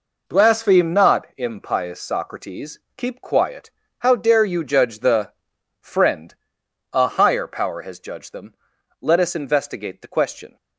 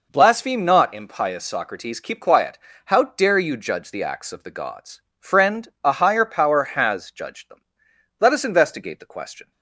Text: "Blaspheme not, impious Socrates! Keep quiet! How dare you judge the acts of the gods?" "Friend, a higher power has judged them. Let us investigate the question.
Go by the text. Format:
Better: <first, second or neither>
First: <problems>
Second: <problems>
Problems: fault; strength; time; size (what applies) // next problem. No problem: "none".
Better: second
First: skips "acts of the gods"; at 5.5 s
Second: none